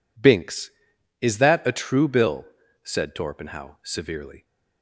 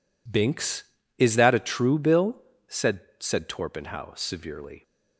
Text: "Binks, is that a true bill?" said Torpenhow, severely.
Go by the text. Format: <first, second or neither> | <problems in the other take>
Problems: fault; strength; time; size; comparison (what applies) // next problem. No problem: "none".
first | says "said" twice; at 3.2 s